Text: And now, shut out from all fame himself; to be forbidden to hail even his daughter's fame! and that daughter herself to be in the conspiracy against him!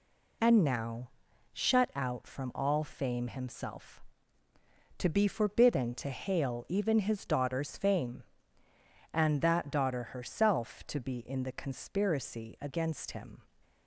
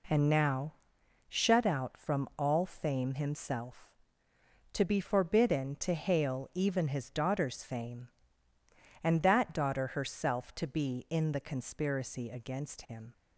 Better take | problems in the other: neither | none

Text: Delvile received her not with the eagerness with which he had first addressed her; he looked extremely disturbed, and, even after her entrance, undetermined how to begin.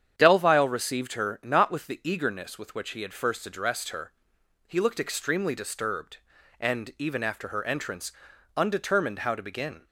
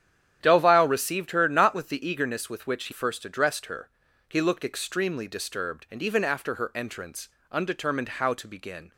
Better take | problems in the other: first | starts louder than the rest; strong; until 1.4 s; 9.5 dB; strong in the first // skips "had"; at 2.9 s

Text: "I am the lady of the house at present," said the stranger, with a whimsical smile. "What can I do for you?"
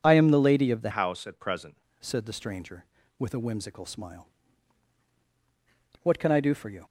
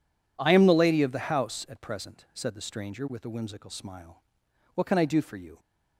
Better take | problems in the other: second | changes voice from "house" to "present"; from 0.9 to 1.7 s; 0.8 s long

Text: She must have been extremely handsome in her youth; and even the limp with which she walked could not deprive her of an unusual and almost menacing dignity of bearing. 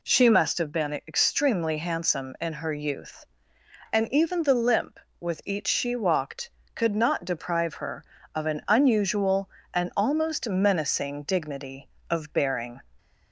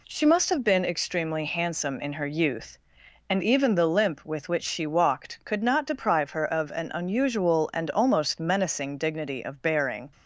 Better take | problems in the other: second | says "each" for "which"; at 5.4 s

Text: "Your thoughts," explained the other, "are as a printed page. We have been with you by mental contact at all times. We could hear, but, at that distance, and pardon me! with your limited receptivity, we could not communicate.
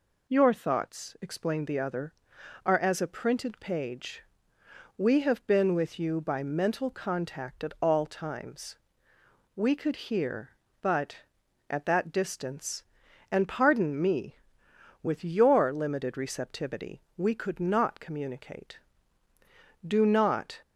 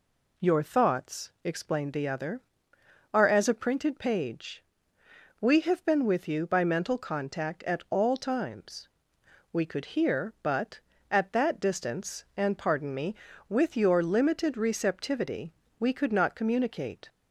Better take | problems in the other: second | goes on to say "Do not"; noticeable; from 19.8 s on; 0.76 s long

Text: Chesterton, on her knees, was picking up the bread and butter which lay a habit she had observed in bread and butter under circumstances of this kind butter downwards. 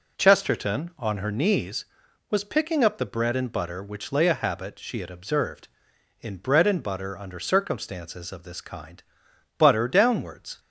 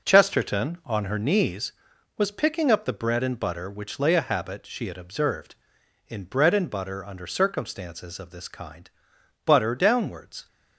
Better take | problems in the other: first | gets quieter; strong; throughout; 8.5 dB // pauses between "kind" and "butter"; noticeable; at 8.9 s; 0.54 s long; noticeable in the first

